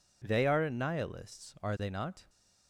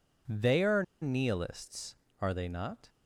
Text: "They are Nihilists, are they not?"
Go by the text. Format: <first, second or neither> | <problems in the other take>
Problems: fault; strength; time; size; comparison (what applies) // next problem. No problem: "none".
first | pauses between "are" and "Nihilists"; slight; at 0.8 s; 0.19 s long